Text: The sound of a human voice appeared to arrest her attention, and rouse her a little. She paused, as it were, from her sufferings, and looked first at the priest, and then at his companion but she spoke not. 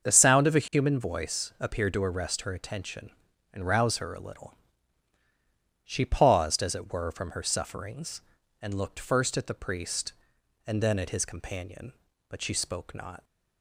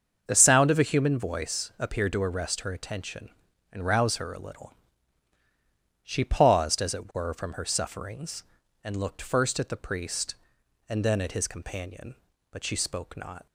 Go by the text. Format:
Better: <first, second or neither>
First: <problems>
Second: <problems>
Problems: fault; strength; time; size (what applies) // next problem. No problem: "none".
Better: neither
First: starts louder than the rest; until 1.1 s; 7 dB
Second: starts louder than the rest; until 1.2 s; 7 dB